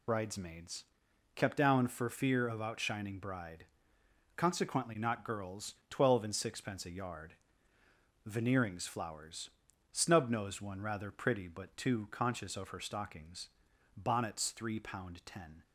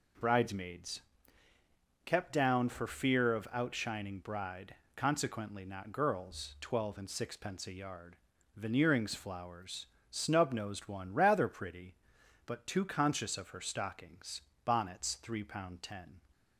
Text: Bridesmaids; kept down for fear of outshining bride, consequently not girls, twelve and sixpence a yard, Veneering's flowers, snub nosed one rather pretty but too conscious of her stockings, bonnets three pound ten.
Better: second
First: loses the start of "Bridesmaids"; at 0.0 s; 50 ms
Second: none

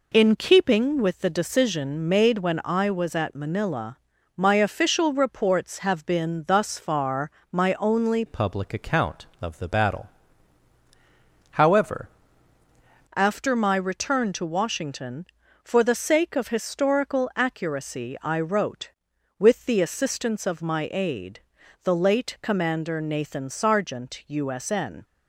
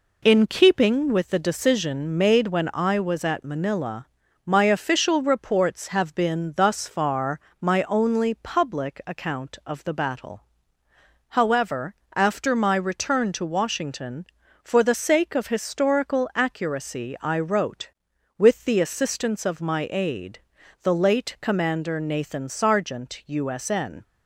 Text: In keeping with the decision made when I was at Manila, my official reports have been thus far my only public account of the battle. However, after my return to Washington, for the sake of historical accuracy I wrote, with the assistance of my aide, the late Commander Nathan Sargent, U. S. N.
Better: second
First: pauses between "far" and "my"; slight; at 7.3 s; 0.20 s long // changes voice from "public" to "However"; from 8.2 to 12.0 s; 3.8 s long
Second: pauses between "far" and "my"; slight; at 7.3 s; 0.20 s long

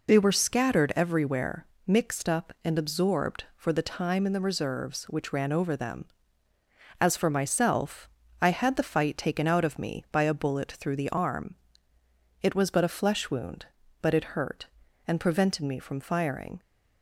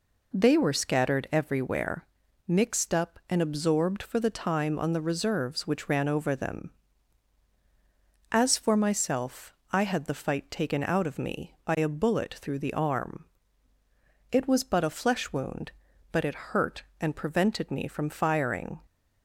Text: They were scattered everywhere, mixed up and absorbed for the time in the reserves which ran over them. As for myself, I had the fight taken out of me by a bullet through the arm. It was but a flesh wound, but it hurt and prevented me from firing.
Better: first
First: none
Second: says "on" for "in"; at 4.7 s

